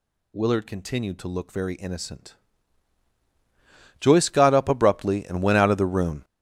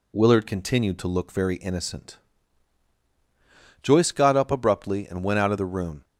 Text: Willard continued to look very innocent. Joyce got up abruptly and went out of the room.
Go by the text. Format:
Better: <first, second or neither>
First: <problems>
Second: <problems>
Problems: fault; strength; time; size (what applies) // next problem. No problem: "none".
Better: second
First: gets louder; strong; throughout; 10.5 dB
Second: none